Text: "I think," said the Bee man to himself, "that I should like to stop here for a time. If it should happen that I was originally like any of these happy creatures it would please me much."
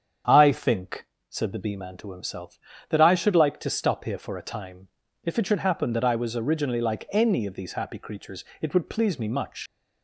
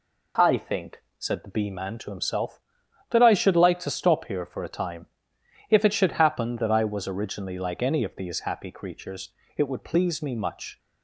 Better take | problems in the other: second | starts louder than the rest; strong; until 1.5 s; 8 dB // pauses between "creatures" and "it"; slight; at 8.4 s; 0.16 s long; slight in the second // leaves "much" unfinished; at 9.6 s; 100 ms

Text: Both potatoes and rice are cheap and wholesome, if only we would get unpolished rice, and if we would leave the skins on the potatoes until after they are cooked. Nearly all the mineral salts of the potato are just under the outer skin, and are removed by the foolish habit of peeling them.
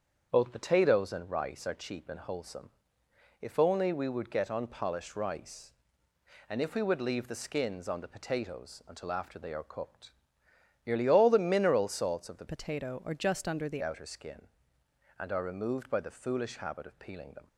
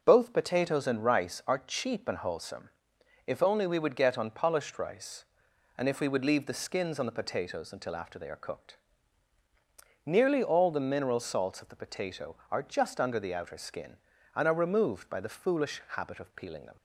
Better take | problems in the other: second | starts louder than the rest; strong; until 1.3 s; 7.5 dB // changes voice from "potato" to "the"; from 12.4 to 13.8 s; 1.4 s long

